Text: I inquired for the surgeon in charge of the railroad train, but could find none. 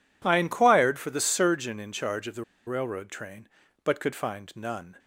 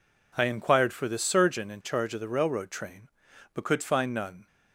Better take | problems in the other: second | pauses between "the" and "railroad"; slight; at 2.4 s; 0.23 s long

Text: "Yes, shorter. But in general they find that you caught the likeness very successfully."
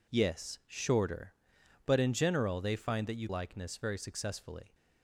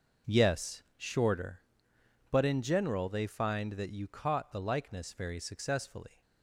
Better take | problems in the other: second | skips "caught the"; at 3.2 s

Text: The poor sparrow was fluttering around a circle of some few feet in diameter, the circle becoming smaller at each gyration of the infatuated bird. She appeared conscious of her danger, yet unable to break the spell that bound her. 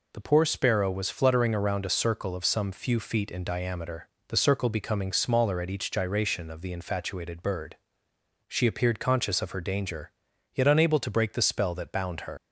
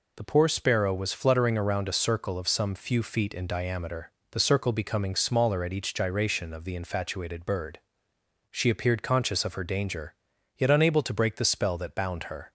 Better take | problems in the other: second | leaves "her" unfinished; at 12.3 s; 105 ms

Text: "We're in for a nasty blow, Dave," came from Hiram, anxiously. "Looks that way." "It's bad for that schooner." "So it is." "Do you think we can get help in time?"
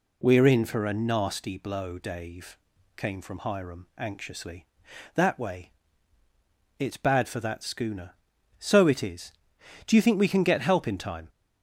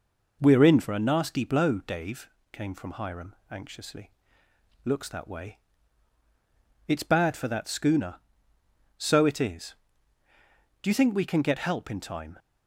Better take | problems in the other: second | skips "Looks"; at 4.9 s

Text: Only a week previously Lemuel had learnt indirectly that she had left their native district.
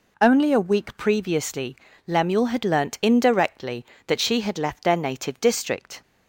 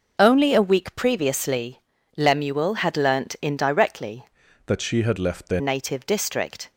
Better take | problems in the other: first | pauses between "previously" and "Lemuel"; slight; at 1.8 s; 0.36 s long; slight in the first // changes voice from "that" to "their"; from 4.6 to 5.5 s; 0.9 s long

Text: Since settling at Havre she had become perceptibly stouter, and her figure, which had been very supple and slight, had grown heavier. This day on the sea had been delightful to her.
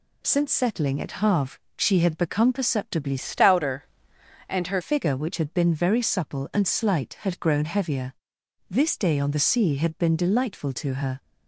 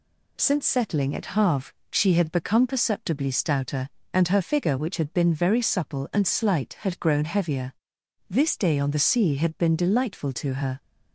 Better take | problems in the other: second | pauses between "Havre" and "she"; slight; at 1.5 s; 0.18 s long; slight in the second // changes voice from "stouter" to "her"; from 3.1 to 4.8 s; 1.7 s long

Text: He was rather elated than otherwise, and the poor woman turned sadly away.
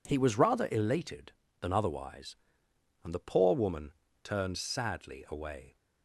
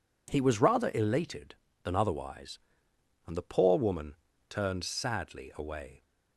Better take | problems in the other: neither | pauses between "woman" and "turned"; slight; the same in both

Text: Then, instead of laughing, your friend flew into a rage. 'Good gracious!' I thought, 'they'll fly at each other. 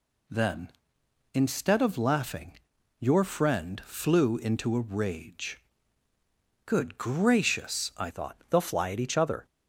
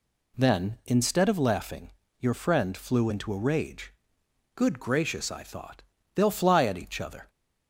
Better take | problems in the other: second | changes voice at "thought"; from 8.1 s on; 1.3 s long

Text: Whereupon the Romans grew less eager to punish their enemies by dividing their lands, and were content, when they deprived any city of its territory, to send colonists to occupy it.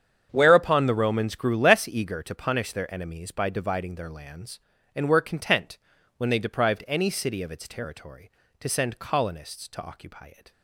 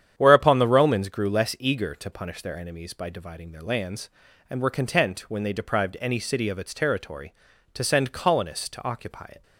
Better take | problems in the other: neither | starts louder than the rest; strong; the same in both

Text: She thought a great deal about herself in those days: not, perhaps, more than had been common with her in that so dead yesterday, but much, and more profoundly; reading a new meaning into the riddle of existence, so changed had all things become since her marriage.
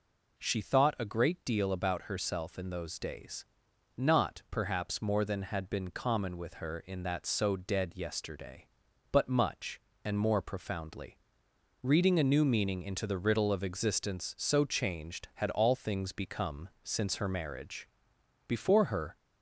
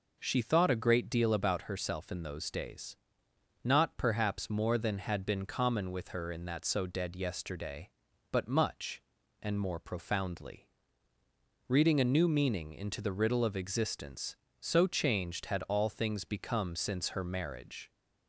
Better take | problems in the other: second | goes on to say "Before her"; noticeable; from 18.4 s on; 0.70 s long

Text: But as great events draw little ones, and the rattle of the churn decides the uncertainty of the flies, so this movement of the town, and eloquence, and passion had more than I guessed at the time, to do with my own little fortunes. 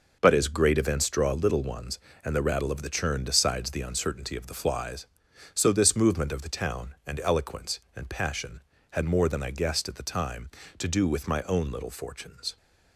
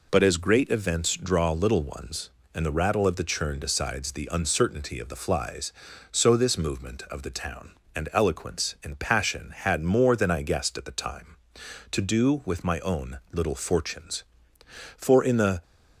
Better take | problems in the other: first | goes on to say "For in the"; noticeable; from 14.9 s on; 0.66 s long

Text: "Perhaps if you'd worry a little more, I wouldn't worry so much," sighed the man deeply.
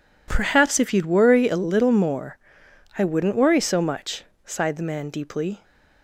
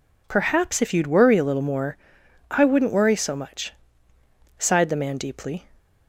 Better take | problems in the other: neither | none

